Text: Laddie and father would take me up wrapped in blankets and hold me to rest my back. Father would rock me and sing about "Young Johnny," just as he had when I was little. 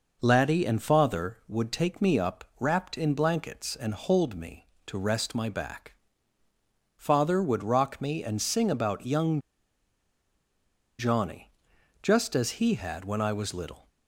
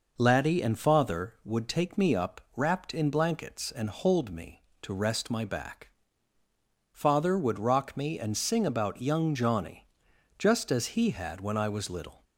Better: second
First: pauses between "Young" and "Johnny"; strong; at 9.4 s; 1.5 s long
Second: none

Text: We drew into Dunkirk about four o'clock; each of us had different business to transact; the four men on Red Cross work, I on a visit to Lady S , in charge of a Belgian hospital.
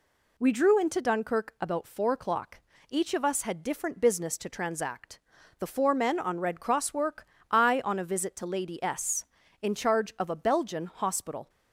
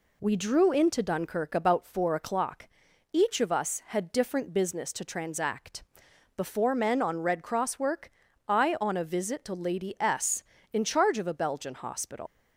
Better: first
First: none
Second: leaves "hospital" unfinished; at 12.2 s; 110 ms

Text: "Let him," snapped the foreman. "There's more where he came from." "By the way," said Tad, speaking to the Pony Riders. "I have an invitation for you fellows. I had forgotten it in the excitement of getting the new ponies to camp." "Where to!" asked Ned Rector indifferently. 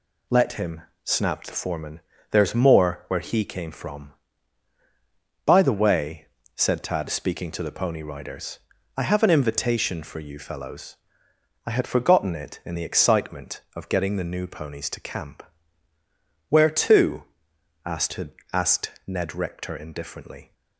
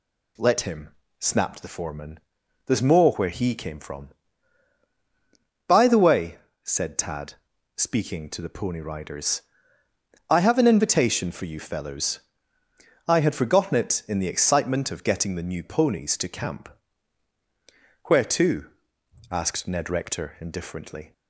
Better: second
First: says "asked" twice; at 18.5 s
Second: none

